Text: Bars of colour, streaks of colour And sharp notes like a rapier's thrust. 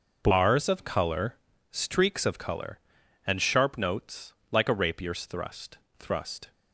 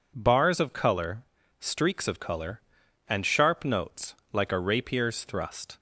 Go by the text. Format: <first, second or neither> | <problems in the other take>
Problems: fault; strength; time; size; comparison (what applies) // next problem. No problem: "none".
second | pauses between "notes" and "like"; slight; at 4.3 s; 0.18 s long; slight in the second // says "thrust" twice; at 5.9 s